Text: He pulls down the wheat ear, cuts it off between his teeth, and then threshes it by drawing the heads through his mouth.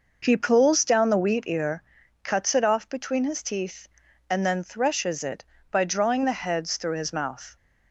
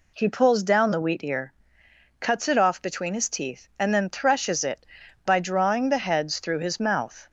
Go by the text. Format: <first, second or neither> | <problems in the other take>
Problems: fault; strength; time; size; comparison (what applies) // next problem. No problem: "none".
neither | none